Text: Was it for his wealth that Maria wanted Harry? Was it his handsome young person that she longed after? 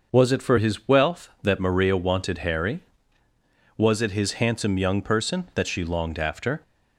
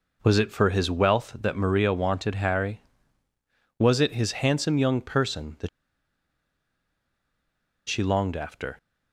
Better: first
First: none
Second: pauses between "that" and "she"; strong; at 5.6 s; 2.2 s long

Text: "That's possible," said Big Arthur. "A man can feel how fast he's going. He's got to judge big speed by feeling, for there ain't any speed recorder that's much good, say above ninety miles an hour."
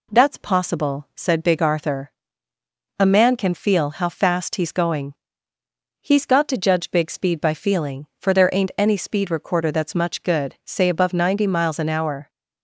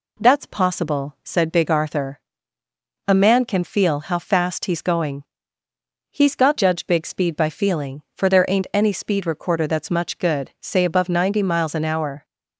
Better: first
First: none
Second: skips "to"; at 6.5 s

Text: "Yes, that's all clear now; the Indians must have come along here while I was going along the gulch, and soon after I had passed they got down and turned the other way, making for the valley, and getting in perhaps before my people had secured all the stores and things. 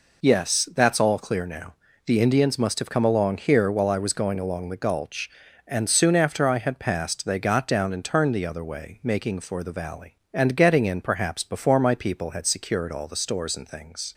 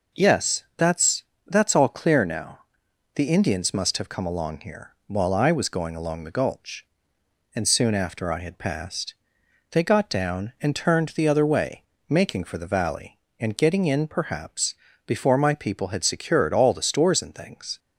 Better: first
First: none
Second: says "that's" twice; at 1.4 s // pauses between "passed" and "they"; noticeable; at 9.1 s; 0.56 s long // pauses between "perhaps" and "before"; slight; at 14.7 s; 0.32 s long

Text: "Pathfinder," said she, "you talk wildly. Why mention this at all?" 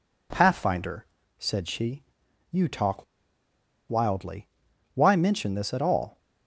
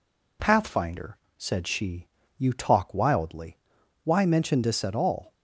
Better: second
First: pauses between "talk" and "wildly"; noticeable; at 3.0 s; 0.84 s long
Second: none

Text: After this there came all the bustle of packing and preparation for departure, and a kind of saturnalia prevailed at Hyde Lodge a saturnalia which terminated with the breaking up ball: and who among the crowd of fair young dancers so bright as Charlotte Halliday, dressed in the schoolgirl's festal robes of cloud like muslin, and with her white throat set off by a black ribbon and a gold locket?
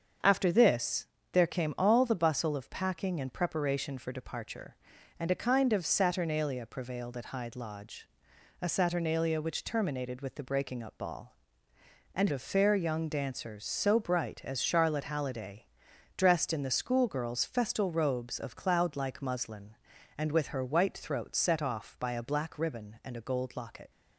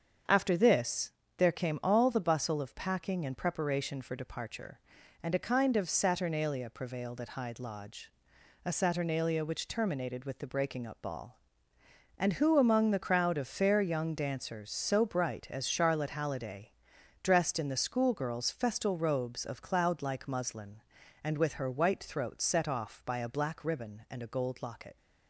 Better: second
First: starts louder than the rest; strong; until 1.4 s; 7 dB // pauses between "this" and "there"; slight; at 1.0 s; 0.26 s long // pauses between "Lodge" and "a"; noticeable; at 8.0 s; 0.56 s long // skips "who among the crowd"; at 12.3 s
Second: starts louder than the rest; strong; until 1.5 s; 7 dB // pauses between "this" and "there"; slight; at 1.1 s; 0.26 s long // pauses between "Lodge" and "a"; noticeable; at 8.0 s; 0.56 s long

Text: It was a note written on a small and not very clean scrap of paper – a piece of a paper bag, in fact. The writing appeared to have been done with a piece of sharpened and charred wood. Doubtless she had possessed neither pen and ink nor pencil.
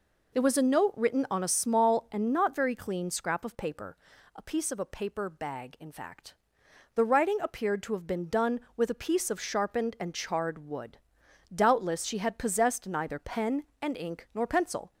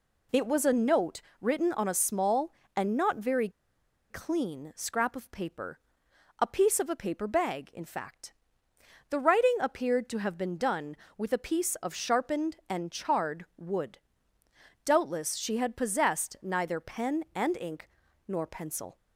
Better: first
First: none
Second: pauses between "note" and "written"; slight; at 1.2 s; 0.20 s long // pauses between "very" and "clean"; noticeable; at 3.4 s; 0.60 s long // pauses between "ink" and "nor"; at 17.8 s; 0.38 s long

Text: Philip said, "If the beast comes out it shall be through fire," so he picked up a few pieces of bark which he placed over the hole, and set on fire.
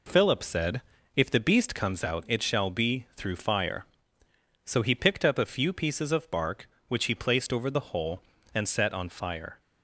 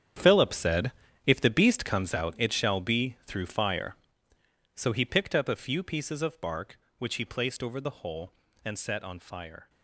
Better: first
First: none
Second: gets quieter; strong; throughout; 13.5 dB

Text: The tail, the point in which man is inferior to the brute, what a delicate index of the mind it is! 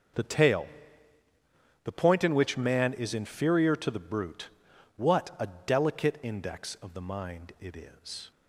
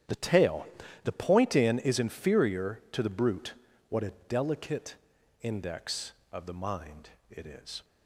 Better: first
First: starts louder than the rest; until 2.3 s; 6.5 dB // pauses between "a" and "delicate"; slight; at 5.4 s; 0.20 s long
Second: starts louder than the rest; strong; until 1.4 s; 10 dB // skips "which man"; at 1.7 s // pauses between "a" and "delicate"; slight; at 4.1 s; 0.16 s long // pauses between "delicate" and "index"; at 4.9 s; 0.44 s long // pauses between "mind" and "it"; slight; at 7.1 s; 0.20 s long

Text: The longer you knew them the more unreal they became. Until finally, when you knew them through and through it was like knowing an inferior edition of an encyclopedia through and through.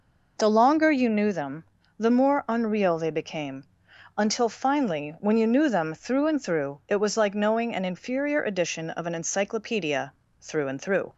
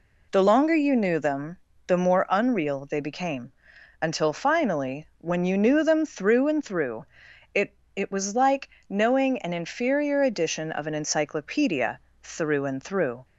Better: first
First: pauses between "them" and "the"; slight; at 1.6 s; 0.34 s long // pauses between "encyclopedia" and "through"; slight; at 10.1 s; 0.26 s long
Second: pauses between "them" and "the"; slight; at 1.5 s; 0.30 s long // pauses between "through" and "it"; noticeable; at 7.0 s; 0.48 s long // says "it" twice; at 7.9 s // pauses between "like" and "knowing"; slight; at 8.6 s; 0.22 s long // pauses between "encyclopedia" and "through"; slight; at 11.9 s; 0.22 s long

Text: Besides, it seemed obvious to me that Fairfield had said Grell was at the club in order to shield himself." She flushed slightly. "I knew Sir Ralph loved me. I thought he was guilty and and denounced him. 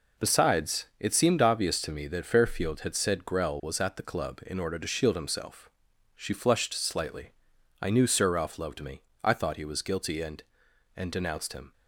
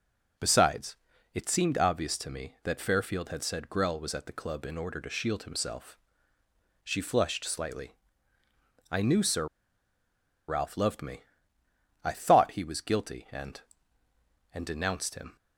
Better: first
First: none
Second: pauses between "Sir" and "Ralph"; at 9.4 s; 1.0 s long

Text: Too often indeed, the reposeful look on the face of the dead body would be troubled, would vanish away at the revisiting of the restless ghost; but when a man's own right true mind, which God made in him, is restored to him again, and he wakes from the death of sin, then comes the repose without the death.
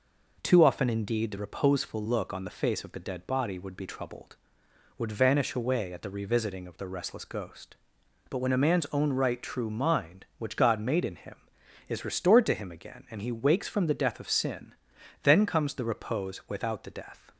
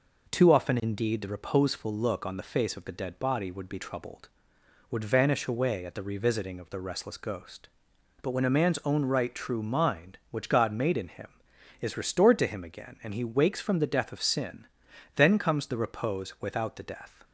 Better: neither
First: none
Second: none

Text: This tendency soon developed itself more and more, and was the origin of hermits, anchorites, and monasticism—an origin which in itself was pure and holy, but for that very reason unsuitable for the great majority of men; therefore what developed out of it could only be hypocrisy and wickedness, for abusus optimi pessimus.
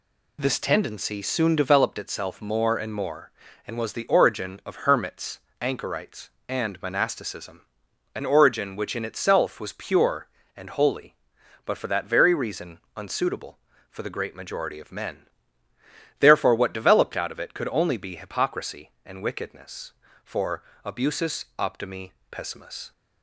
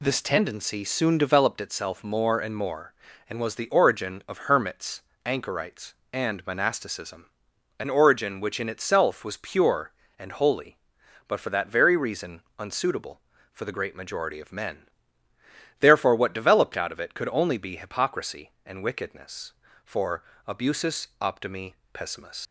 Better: first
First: pauses between "reason" and "unsuitable"; slight; at 12.7 s; 0.18 s long // pauses between "for" and "abusus"; slight; at 20.6 s; 0.22 s long // pauses between "optimi" and "pessimus"; slight; at 22.1 s; 0.18 s long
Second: pauses between "reason" and "unsuitable"; slight; at 12.4 s; 0.18 s long // pauses between "for" and "abusus"; slight; at 20.2 s; 0.24 s long // pauses between "optimi" and "pessimus"; slight; at 21.7 s; 0.18 s long // leaves "pessimus" unfinished; at 22.4 s; 90 ms

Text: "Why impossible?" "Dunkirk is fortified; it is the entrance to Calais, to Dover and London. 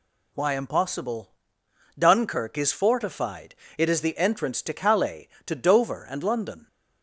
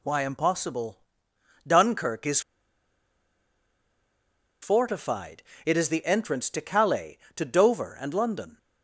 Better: first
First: none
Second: pauses between "is" and "fortified"; strong; at 2.4 s; 2.2 s long

